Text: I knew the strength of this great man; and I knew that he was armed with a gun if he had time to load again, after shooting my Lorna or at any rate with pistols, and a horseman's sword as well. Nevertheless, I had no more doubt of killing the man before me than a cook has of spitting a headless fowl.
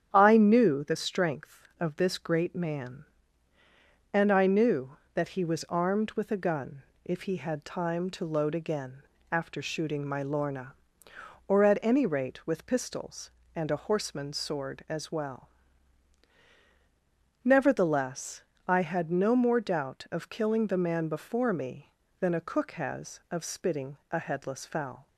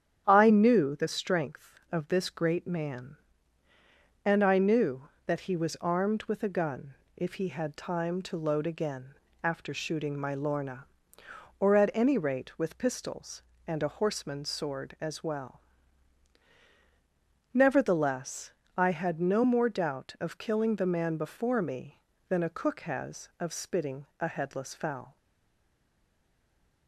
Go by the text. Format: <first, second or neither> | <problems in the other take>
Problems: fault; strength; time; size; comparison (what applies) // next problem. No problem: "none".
first | starts louder than the rest; strong; until 1.2 s; 8.5 dB; strong in the first // pauses between "gun" and "if"; slight; at 6.9 s; 0.22 s long; slight in the first // stays silent after the last word; noticeable; from 25.1 s on; 1.7 s long